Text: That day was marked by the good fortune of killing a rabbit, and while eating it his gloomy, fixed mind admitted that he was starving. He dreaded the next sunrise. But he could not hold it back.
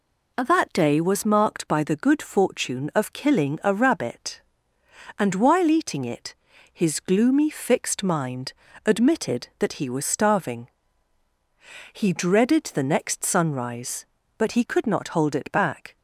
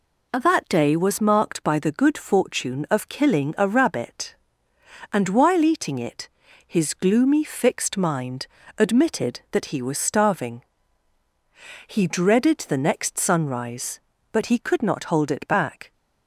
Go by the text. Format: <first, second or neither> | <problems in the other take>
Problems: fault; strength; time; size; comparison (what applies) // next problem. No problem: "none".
neither | pauses between "it" and "his"; the same in both // pauses between "mind" and "admitted"; slight; the same in both